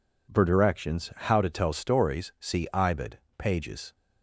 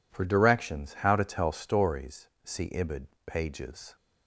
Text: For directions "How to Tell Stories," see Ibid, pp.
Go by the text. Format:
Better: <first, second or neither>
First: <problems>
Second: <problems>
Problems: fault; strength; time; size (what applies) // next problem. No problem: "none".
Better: neither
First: none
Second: none